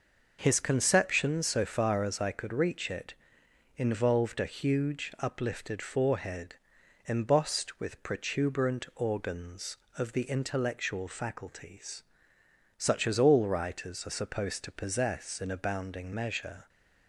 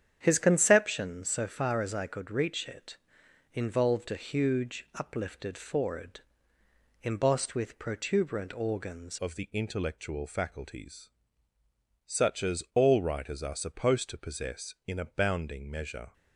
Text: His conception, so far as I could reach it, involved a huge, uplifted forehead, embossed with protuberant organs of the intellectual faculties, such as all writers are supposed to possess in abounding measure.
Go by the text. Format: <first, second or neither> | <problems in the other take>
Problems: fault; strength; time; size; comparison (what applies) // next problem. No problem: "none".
first | starts louder than the rest; strong; until 1.2 s; 9 dB // changes voice at "of"; from 9.1 s on; 7.0 s long